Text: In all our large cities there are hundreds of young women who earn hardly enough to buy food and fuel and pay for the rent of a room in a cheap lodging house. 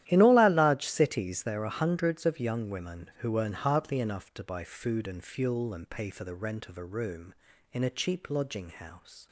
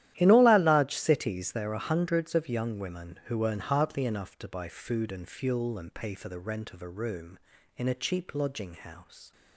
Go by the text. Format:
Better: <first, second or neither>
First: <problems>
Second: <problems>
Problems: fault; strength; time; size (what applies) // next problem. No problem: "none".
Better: neither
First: starts louder than the rest; strong; until 1.0 s; 12.5 dB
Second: starts louder than the rest; strong; until 1.1 s; 12.5 dB